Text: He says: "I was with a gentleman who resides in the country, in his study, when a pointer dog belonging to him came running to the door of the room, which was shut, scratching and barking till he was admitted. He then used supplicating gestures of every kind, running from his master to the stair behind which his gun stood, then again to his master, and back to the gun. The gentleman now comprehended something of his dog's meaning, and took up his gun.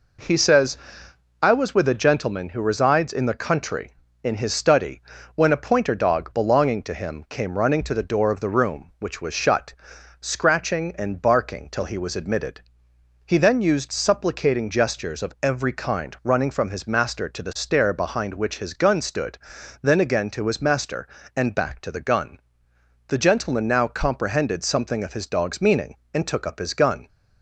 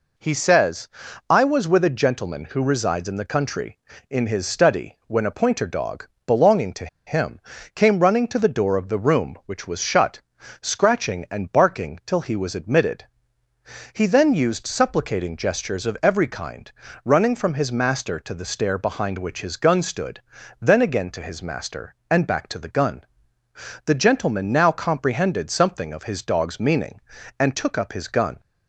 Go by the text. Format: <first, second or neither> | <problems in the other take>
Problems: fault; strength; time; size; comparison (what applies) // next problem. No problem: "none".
first | pauses between "dog" and "belonging"; slight; at 6.0 s; 0.18 s long // pauses between "to" and "him"; slight; at 6.8 s; 0.20 s long // pauses between "him" and "came"; at 7.3 s; 0.38 s long